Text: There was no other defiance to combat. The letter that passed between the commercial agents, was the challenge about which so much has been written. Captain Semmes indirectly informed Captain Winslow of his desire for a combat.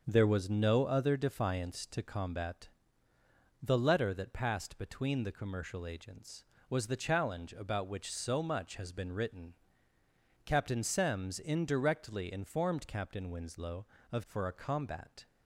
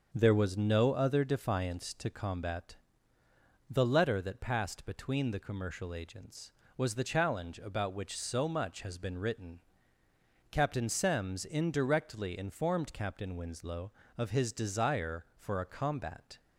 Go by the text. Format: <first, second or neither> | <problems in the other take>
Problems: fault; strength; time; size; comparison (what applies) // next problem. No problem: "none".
second | starts louder than the rest; until 1.0 s; 6 dB; also in the second // skips "his desire"; at 14.2 s